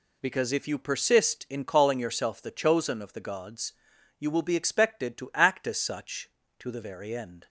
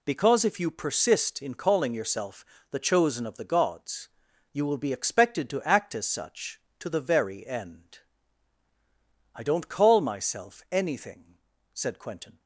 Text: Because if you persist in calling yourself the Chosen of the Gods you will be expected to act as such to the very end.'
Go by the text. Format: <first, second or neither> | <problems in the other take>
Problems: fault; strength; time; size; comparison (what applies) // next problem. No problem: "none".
first | pauses between "yourself" and "the"; slight; at 2.4 s; 0.28 s long // pauses between "Gods" and "you"; noticeable; at 4.0 s; 0.46 s long; noticeable in the first // goes on to say "I don't call myself anything said Quentin"; strong; from 9.3 s on; 3.0 s long